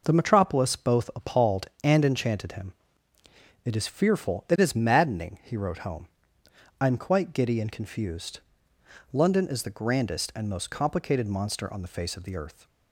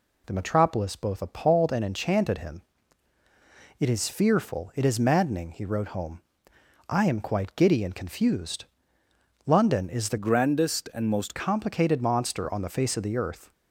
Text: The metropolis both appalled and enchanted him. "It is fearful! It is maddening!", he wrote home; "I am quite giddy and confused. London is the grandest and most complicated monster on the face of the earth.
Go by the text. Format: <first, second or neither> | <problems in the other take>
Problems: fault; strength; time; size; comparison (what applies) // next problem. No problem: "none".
first | changes voice from "grandest" to "most"; from 10.1 to 11.3 s; 1.2 s long